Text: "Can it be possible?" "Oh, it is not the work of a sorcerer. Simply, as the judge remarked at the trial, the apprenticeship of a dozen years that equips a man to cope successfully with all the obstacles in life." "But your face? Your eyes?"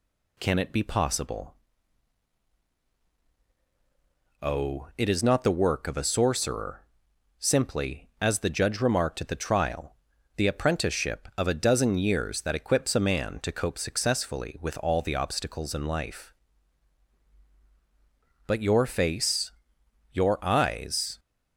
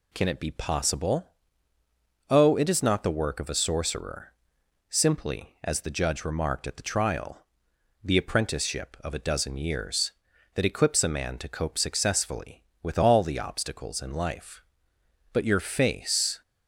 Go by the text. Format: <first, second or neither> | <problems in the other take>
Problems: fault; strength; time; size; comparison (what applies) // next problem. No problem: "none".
first | stops before "Your eyes"; at 16.4 s